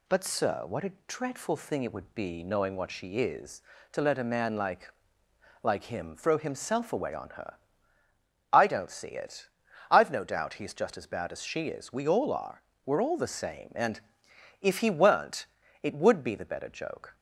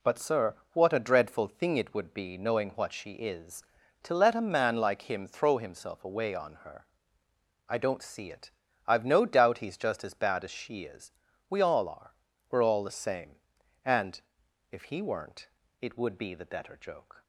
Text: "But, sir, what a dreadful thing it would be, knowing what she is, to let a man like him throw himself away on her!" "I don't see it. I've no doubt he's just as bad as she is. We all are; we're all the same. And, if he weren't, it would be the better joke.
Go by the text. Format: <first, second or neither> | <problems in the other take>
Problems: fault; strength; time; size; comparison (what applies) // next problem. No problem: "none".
second | pauses between "a" and "dreadful"; slight; at 0.9 s; 0.16 s long // says "like" twice; at 5.6 s